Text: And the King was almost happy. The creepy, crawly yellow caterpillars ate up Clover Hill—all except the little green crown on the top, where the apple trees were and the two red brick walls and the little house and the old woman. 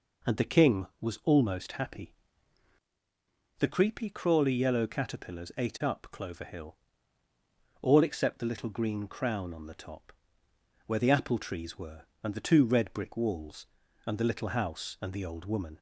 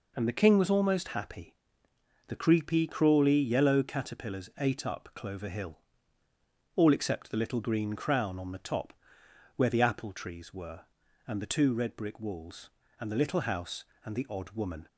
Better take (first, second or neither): first